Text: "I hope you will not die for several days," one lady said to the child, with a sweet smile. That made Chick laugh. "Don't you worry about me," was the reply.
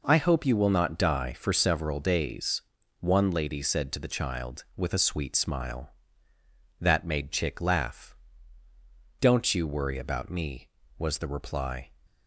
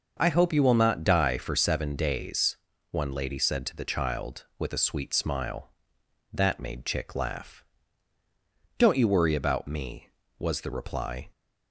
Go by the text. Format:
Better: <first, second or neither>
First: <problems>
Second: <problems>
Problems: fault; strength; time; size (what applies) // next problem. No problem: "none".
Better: first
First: none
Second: says "seven" for "several"; at 1.5 s